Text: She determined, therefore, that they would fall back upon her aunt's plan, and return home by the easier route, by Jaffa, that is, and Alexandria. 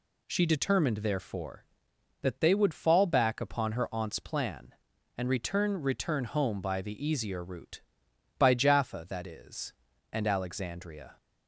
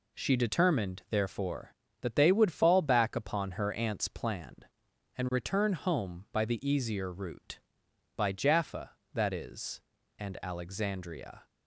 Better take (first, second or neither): second